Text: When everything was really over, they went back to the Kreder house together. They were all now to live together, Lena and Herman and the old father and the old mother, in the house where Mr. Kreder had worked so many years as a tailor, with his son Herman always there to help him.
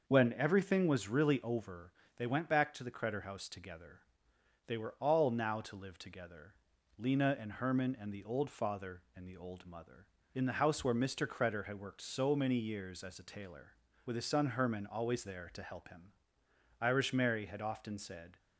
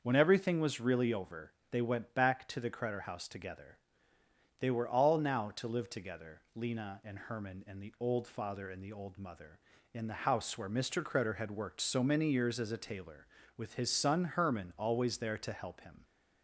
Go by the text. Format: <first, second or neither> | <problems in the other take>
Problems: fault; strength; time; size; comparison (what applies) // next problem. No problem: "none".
second | starts louder than the rest; noticeable; until 1.1 s; 6 dB; also in the second // goes on to say "Irish Mary had often said"; from 16.8 s on; 1.5 s long